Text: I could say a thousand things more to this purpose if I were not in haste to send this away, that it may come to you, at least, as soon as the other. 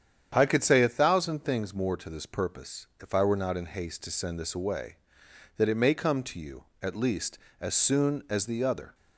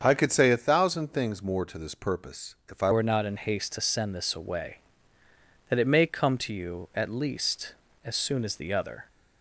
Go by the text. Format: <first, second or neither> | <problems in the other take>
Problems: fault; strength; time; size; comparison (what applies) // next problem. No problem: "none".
first | starts louder than the rest; until 1.0 s; 7 dB; strong in the first // changes voice at "were"; from 2.9 s on; 6.1 s long